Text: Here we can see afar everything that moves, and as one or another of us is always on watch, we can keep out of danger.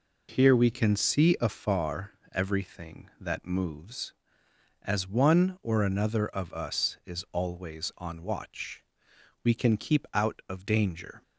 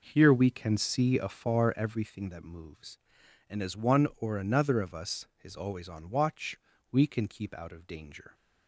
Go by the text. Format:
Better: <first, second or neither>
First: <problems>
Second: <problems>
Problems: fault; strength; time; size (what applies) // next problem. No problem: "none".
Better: second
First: pauses between "afar" and "everything"; slight; at 2.1 s; 0.20 s long // skips "and"; at 4.4 s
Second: none